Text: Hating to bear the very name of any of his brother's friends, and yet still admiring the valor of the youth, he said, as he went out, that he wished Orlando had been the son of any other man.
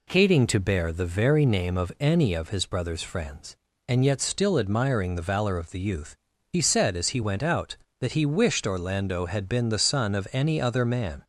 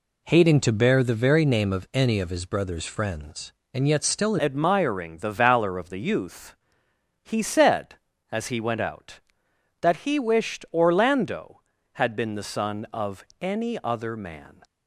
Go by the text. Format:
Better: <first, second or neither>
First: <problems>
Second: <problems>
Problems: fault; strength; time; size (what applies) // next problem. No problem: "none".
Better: first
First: none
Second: changes voice at "admiring"; from 4.3 s on; 10.3 s long // pauses between "of" and "any"; slight; at 13.2 s; 0.20 s long